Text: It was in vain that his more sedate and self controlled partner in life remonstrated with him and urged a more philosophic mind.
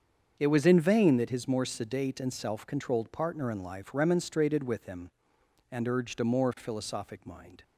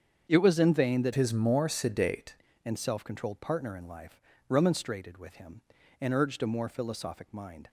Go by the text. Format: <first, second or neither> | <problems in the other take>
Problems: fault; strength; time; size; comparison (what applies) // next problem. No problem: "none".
first | starts louder than the rest; strong; until 1.3 s; 7.5 dB; also in the first // changes voice from "his" to "sedate"; from 1.1 to 2.3 s; 1.2 s long // pauses between "life" and "remonstrated"; slight; at 4.1 s; 0.30 s long